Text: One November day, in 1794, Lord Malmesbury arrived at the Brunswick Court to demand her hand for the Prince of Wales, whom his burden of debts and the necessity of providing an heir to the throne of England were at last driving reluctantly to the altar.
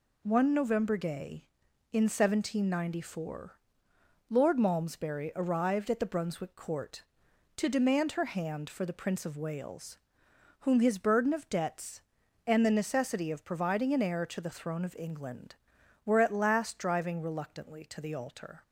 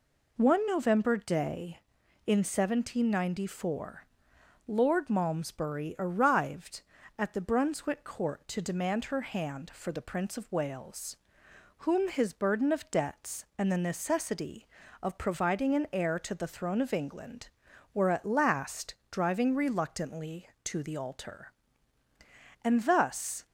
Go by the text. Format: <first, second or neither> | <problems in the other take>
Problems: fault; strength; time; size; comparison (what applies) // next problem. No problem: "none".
first | pauses between "last" and "driving"; slight; at 18.9 s; 0.18 s long // goes on to say "And thus"; noticeable; from 22.6 s on; 0.84 s long